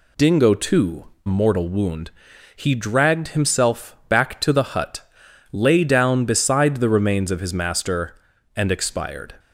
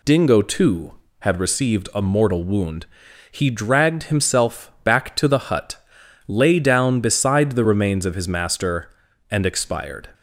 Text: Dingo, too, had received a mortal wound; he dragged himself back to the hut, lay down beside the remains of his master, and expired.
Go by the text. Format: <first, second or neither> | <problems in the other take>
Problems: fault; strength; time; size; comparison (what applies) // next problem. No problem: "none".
second | skips "had received a"; at 1.1 s